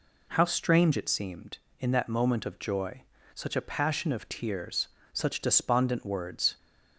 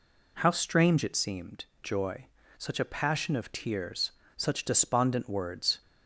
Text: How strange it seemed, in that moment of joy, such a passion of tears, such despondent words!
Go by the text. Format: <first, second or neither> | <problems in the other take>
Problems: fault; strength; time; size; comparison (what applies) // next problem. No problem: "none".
first | skips "in that moment of"; at 1.7 s